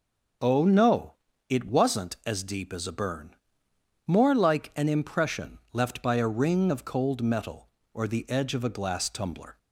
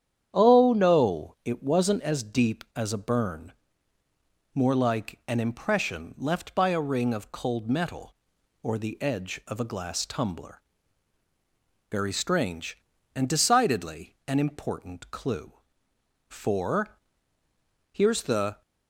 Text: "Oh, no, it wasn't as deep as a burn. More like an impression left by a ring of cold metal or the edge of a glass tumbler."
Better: first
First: none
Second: starts louder than the rest; strong; until 1.3 s; 9 dB // goes on to say "Very strange and decidedly an important clue For here's the"; strong; from 11.8 s on; 6.7 s long

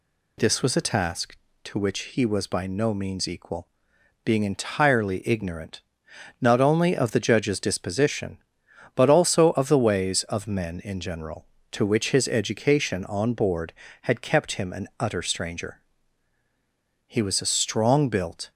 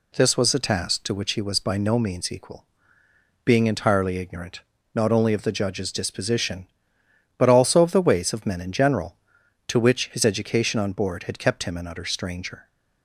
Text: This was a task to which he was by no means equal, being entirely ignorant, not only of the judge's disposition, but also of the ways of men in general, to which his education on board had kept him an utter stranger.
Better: second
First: goes on to say "He was a strong built"; from 17.0 s on; 1.4 s long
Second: none

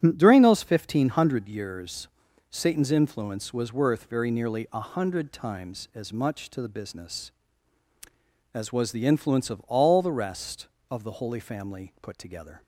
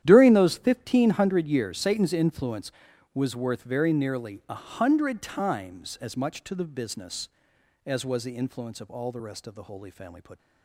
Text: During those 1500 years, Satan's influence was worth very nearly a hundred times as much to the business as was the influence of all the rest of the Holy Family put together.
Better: first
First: starts louder than the rest; strong; until 1.0 s; 8 dB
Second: starts louder than the rest; strong; until 1.0 s; 11 dB // stops before "together"; at 10.3 s

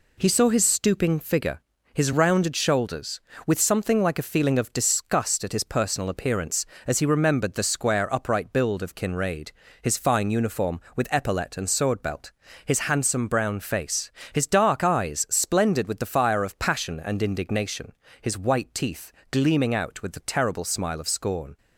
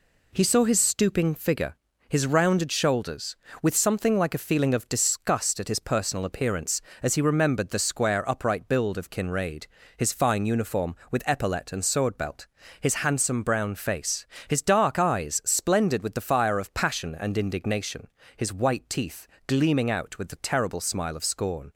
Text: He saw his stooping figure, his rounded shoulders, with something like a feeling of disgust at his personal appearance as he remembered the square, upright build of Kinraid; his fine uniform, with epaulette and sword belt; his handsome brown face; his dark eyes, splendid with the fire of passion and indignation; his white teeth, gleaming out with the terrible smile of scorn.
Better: neither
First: none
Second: none

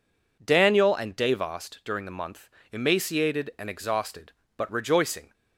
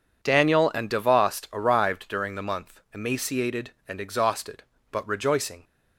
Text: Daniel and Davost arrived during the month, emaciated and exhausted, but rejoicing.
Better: second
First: skips "arrived"; at 1.8 s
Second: none

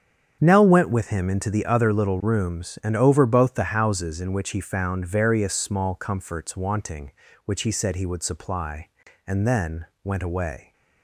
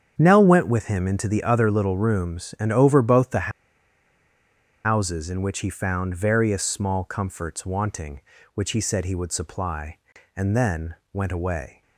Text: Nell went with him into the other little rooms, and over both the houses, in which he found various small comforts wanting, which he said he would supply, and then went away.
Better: first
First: starts louder than the rest; strong; until 1.4 s; 8 dB // pauses between "then" and "went"; slight; at 9.8 s; 0.18 s long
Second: starts louder than the rest; strong; until 1.1 s; 8 dB // pauses between "the" and "houses"; strong; at 3.5 s; 1.3 s long // pauses between "then" and "went"; slight; at 10.9 s; 0.18 s long

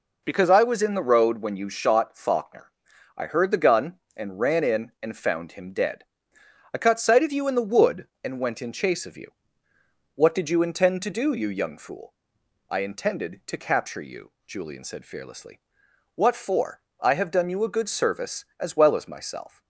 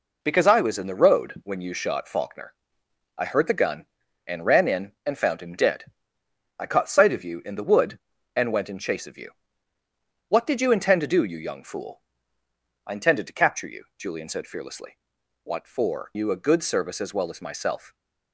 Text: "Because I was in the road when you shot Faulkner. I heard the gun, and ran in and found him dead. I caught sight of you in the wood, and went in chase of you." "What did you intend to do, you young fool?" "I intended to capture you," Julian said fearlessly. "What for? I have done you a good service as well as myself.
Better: first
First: none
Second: skips "I have done"; at 16.1 s

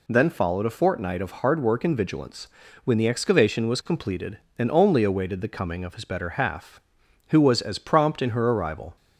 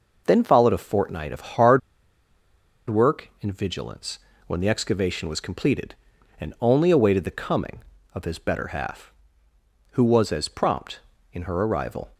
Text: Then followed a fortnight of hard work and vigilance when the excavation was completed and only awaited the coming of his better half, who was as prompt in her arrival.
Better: first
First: pauses between "vigilance" and "when"; slight; at 2.4 s; 0.36 s long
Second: pauses between "hard" and "work"; at 1.8 s; 1.1 s long // pauses between "vigilance" and "when"; slight; at 4.1 s; 0.28 s long

